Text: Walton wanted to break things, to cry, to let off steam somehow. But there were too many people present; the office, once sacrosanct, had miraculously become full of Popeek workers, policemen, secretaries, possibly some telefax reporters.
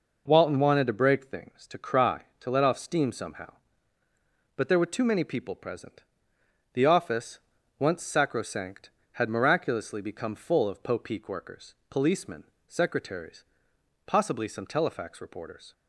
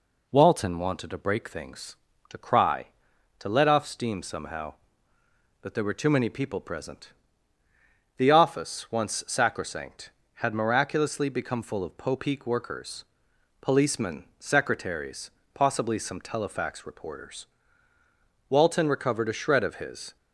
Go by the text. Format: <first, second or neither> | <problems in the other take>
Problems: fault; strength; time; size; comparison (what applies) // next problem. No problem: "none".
first | goes on to say "Walton recovered a shred of his"; from 18.5 s on; 1.6 s long